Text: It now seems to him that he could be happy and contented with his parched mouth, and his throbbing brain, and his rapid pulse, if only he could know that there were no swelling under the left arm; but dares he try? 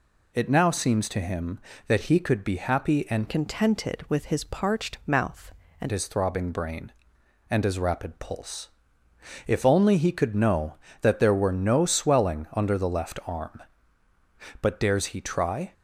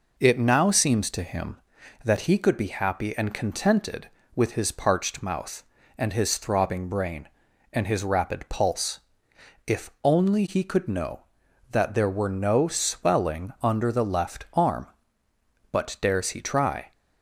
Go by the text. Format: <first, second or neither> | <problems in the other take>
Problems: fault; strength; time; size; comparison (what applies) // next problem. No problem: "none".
second | changes voice from "contented" to "and"; from 3.2 to 5.9 s; 2.7 s long